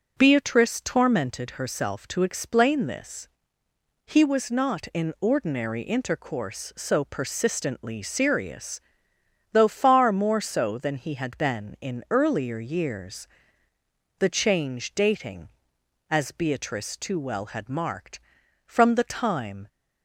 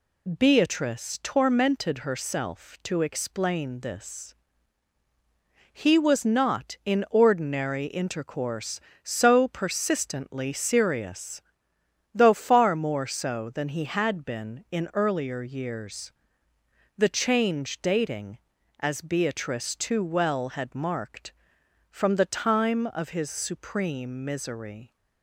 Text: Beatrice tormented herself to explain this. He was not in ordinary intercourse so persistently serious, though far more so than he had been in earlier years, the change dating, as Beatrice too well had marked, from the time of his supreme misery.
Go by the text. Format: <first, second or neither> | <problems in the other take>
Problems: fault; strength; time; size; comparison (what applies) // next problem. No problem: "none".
second | stops before "of his supreme misery"; at 19.6 s